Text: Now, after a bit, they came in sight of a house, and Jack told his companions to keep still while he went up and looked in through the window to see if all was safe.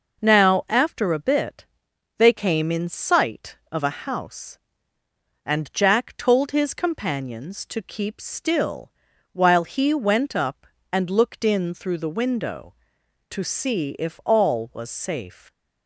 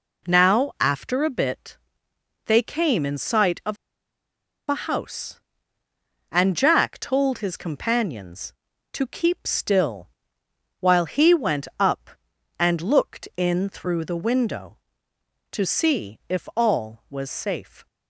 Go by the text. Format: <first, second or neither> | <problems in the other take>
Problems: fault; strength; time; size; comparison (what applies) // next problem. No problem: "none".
first | pauses between "of" and "a"; noticeable; at 3.7 s; 0.92 s long // pauses between "still" and "while"; noticeable; at 10.1 s; 0.70 s long; also in the first